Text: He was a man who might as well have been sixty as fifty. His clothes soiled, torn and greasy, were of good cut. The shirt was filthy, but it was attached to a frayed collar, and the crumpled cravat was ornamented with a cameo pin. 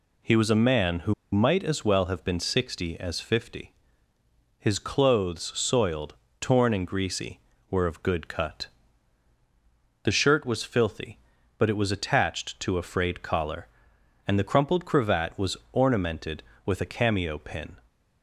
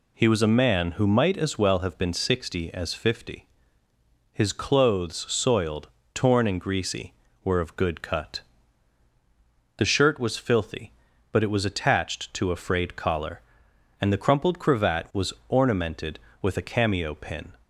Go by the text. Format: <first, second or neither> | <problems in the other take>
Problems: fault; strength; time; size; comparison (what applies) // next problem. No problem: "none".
second | pauses between "who" and "might"; slight; at 1.1 s; 0.18 s long // pauses between "was" and "ornamented"; slight; at 15.5 s; 0.16 s long; slight in the second